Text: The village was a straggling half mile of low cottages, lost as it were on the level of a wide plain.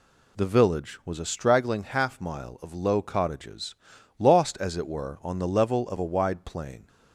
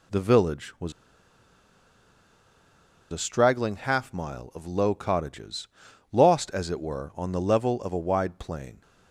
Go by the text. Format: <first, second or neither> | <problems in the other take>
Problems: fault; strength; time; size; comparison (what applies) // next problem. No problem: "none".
first | pauses between "was" and "a"; strong; at 0.9 s; 2.2 s long